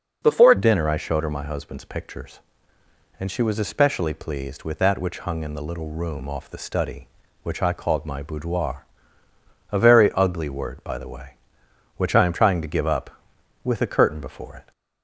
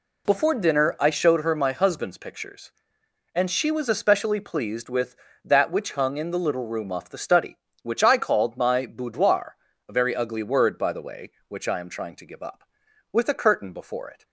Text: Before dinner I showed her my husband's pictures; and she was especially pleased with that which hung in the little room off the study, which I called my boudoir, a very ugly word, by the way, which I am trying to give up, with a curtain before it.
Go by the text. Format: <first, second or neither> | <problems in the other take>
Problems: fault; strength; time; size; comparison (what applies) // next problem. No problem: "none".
second | changes voice at "dinner"; from 0.5 s on; 14.2 s long